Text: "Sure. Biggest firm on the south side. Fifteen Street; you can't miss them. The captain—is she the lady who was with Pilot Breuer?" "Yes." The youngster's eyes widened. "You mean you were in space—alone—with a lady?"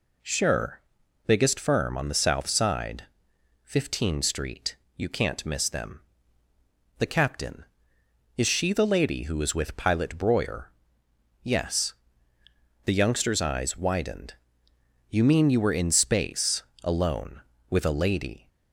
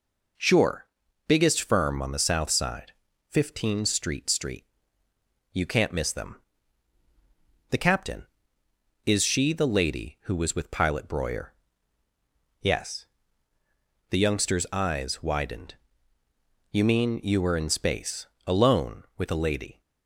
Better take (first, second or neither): first